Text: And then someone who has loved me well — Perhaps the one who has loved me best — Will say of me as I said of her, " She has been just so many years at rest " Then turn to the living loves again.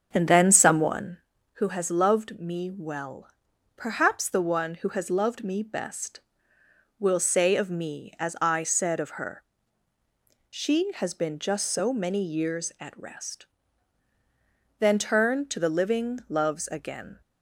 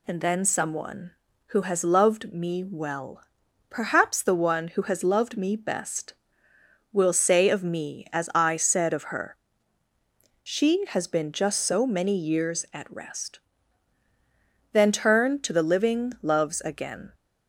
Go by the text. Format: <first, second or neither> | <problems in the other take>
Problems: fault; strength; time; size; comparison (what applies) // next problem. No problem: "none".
second | starts louder than the rest; strong; until 1.2 s; 7 dB